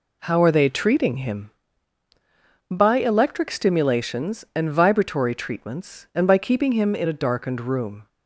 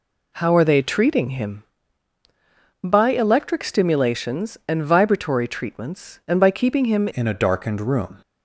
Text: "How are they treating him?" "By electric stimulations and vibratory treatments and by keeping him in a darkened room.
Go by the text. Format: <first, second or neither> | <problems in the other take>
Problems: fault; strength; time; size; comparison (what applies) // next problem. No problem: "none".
first | changes voice at "in"; from 7.1 s on; 1.0 s long